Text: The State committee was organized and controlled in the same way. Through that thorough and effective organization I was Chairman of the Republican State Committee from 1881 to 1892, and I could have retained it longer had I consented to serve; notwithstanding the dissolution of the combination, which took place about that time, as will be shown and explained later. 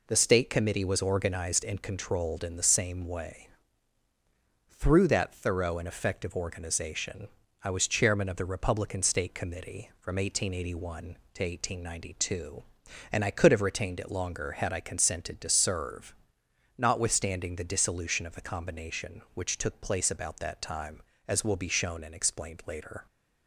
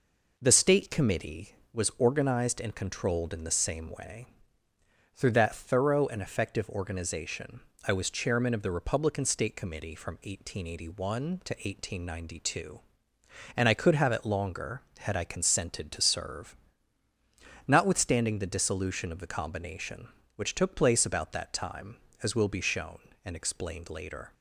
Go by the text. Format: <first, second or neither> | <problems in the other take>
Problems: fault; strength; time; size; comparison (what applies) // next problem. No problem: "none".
first | pauses between "organization" and "I"; slight; at 7.6 s; 0.26 s long; slight in the first // skips "retained"; at 14.1 s